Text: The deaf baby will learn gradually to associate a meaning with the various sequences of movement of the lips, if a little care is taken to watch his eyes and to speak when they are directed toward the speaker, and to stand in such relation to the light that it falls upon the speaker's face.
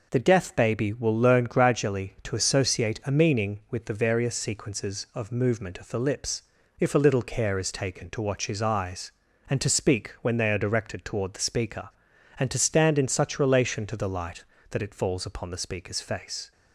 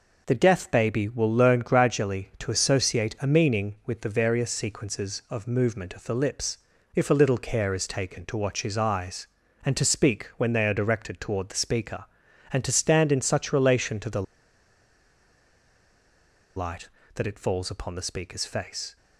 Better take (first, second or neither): first